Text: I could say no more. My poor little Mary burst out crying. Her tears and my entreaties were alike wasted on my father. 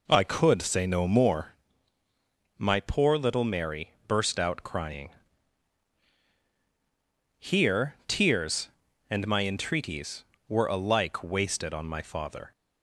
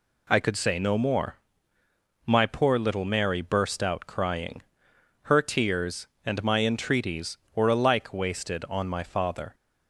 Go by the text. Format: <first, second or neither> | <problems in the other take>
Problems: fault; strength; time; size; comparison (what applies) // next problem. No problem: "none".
second | pauses between "Mary" and "burst"; slight; at 3.8 s; 0.18 s long // says "Here" for "Her"; at 7.3 s